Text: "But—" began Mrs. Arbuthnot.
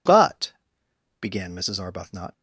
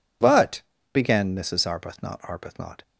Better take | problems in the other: first | says "Arbuthnot" twice; at 2.1 s

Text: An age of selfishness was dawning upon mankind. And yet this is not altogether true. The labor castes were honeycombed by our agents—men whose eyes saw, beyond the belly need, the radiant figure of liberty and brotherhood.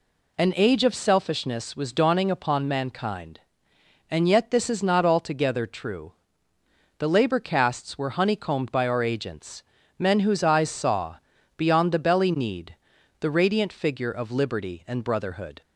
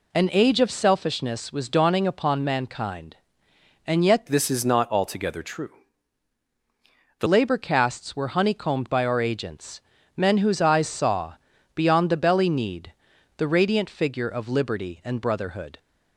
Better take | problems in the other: first | changes voice from "this" to "The"; from 4.2 to 7.2 s; 3.0 s long

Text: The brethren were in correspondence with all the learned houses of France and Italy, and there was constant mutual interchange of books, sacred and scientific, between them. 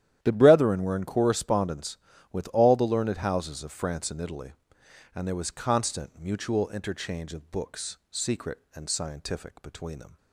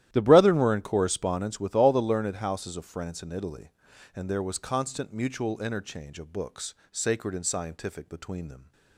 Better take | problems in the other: second | starts louder than the rest; strong; until 1.2 s; 11.5 dB; strong in the second // says "secret" for "sacred"; at 8.1 s

